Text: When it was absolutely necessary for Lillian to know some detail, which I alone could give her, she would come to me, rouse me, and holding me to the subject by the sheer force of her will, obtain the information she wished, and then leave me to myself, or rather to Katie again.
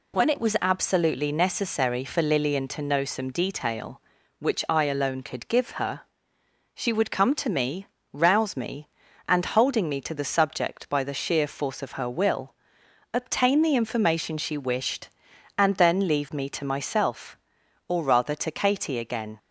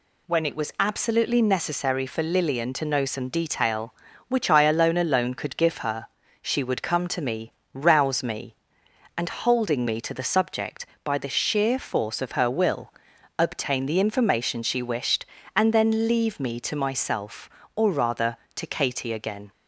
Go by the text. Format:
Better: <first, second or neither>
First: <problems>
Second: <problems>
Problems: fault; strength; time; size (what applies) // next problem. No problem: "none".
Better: first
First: none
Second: says "alone" twice; at 4.9 s